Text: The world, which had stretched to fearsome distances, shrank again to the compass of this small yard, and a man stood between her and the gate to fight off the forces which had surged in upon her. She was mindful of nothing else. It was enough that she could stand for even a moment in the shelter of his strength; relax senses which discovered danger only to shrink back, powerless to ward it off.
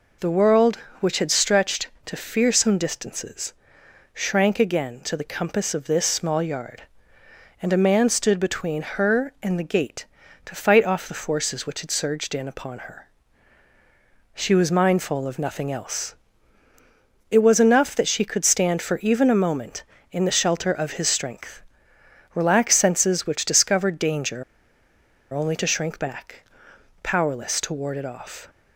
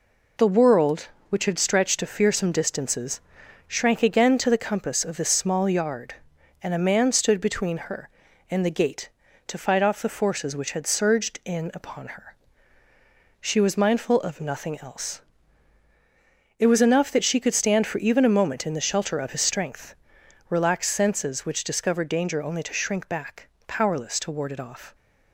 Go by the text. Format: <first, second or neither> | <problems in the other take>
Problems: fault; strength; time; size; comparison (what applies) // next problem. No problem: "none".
second | pauses between "danger" and "only"; noticeable; at 24.4 s; 0.90 s long